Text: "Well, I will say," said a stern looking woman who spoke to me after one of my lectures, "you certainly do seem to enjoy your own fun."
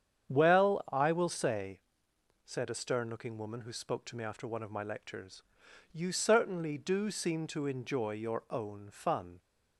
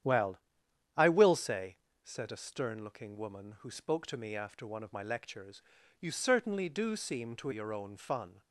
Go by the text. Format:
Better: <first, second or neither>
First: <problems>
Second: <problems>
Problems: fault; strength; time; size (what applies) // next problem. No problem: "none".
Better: first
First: starts louder than the rest; strong; until 1.3 s; 8.5 dB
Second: starts louder than the rest; strong; until 1.6 s; 9.5 dB // skips "enjoy"; at 7.5 s